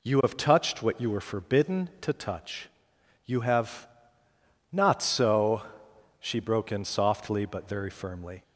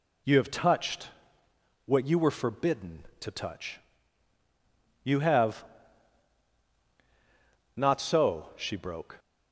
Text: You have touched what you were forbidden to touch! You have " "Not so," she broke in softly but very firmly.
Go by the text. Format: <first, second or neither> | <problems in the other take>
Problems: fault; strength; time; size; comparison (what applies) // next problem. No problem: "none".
first | pauses between "touched" and "what"; noticeable; at 1.0 s; 0.76 s long // stops before "in softly but very firmly"; at 9.1 s